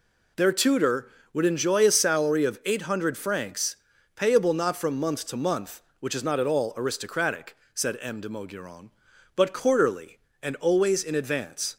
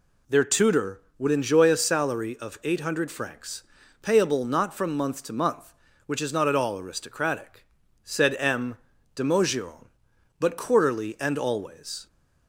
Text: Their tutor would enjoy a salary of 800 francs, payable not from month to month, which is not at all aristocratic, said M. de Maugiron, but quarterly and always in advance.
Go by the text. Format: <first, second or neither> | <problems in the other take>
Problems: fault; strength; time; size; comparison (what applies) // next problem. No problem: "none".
first | stops before "in advance"; at 12.0 s